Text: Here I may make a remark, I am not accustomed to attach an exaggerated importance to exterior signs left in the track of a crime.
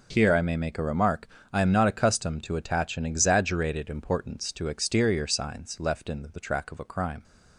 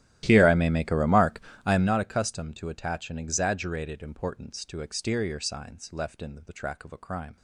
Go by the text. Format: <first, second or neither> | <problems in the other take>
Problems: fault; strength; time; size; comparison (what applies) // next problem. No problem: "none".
first | starts louder than the rest; strong; until 2.0 s; 14 dB